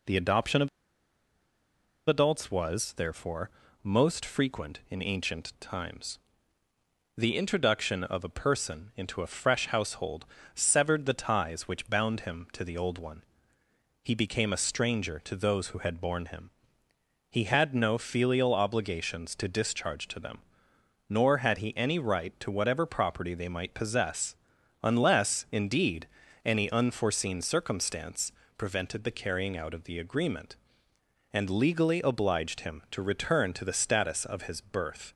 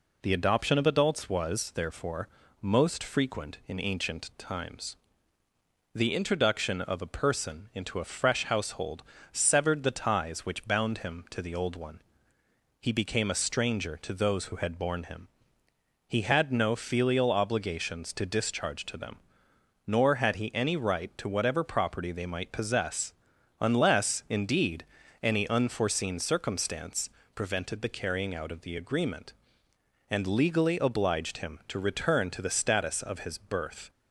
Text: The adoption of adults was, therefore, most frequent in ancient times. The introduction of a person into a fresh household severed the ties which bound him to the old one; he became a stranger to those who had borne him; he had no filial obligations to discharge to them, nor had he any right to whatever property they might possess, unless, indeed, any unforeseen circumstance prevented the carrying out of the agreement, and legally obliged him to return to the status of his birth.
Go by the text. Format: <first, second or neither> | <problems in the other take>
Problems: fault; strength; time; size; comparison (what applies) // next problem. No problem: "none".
second | pauses between "of" and "adults"; strong; at 0.6 s; 1.3 s long // pauses between "household" and "severed"; slight; at 10.2 s; 0.30 s long; slight in the second // pauses between "circumstance" and "prevented"; slight; at 28.3 s; 0.26 s long; slight in the second